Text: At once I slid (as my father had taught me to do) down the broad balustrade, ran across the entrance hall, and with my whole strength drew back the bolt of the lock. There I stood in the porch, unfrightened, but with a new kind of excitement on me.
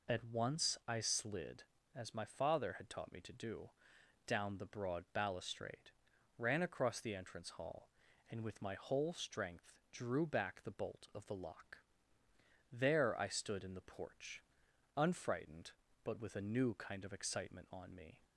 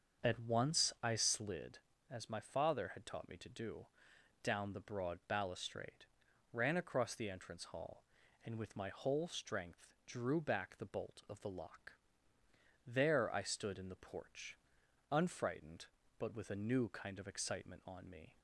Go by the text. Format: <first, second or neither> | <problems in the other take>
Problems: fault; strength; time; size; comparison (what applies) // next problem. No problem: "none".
first | starts louder than the rest; until 1.6 s; 6.5 dB // pauses between "strength" and "drew"; slight; at 9.8 s; 0.20 s long; slight in the first